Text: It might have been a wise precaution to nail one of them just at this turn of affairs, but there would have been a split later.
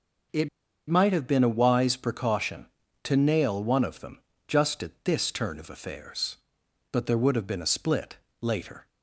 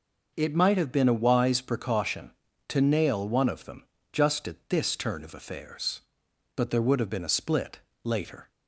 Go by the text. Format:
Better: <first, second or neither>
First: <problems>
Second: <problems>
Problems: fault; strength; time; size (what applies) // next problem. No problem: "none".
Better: second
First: pauses between "It" and "might"; at 0.4 s; 0.41 s long // pauses between "them" and "just"; slight; at 4.1 s; 0.28 s long // pauses between "split" and "later"; slight; at 8.1 s; 0.24 s long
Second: pauses between "them" and "just"; slight; at 3.8 s; 0.28 s long // pauses between "split" and "later"; slight; at 7.8 s; 0.24 s long